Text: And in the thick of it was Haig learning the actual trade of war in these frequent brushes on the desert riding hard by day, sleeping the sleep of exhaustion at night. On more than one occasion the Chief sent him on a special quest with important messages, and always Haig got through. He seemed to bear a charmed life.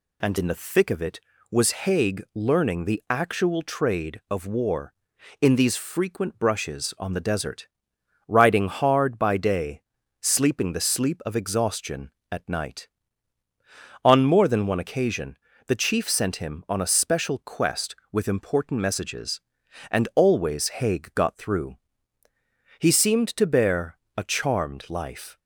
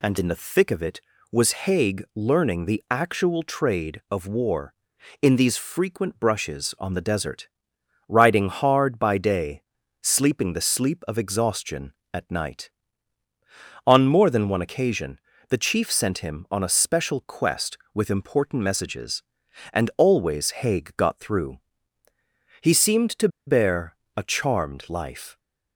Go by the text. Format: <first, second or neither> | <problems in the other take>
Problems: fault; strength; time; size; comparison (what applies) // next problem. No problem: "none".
first | pauses between "desert" and "riding"; noticeable; at 7.4 s; 0.60 s long; noticeable in the first // pauses between "occasion" and "the"; slight; at 15.1 s; 0.30 s long; slight in the first // pauses between "to" and "bear"; slight; at 23.2 s; 0.19 s long // pauses between "bear" and "a"; slight; at 23.9 s; 0.20 s long; slight in the first